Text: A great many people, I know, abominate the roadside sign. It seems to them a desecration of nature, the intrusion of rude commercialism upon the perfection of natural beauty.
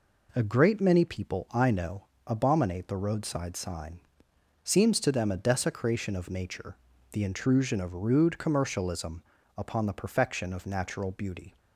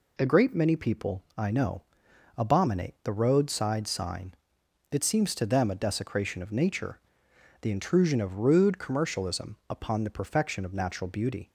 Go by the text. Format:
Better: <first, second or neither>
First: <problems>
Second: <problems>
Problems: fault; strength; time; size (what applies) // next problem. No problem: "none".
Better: second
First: skips "It"; at 4.3 s // pauses between "commercialism" and "upon"; slight; at 9.2 s; 0.32 s long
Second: none